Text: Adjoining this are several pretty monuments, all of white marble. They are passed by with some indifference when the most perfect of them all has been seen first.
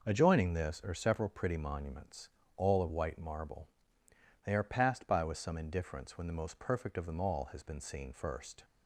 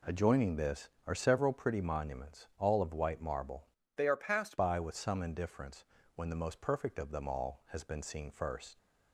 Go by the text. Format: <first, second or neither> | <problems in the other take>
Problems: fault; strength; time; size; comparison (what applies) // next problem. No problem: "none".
first | changes voice from "They" to "passed"; from 3.9 to 4.5 s; 0.6 s long // pauses between "indifference" and "when"; slight; at 5.8 s; 0.32 s long